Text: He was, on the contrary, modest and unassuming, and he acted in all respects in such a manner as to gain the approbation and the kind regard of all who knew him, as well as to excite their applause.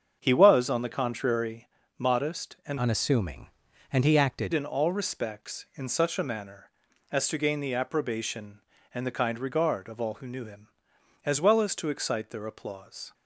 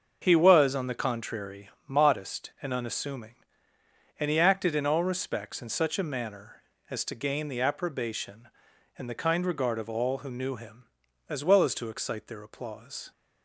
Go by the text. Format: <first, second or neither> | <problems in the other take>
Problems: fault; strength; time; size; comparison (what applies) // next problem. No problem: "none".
second | starts louder than the rest; strong; until 1.2 s; 7 dB; also in the second // changes voice from "unassuming" to "acted"; from 2.7 to 4.5 s; 1.8 s long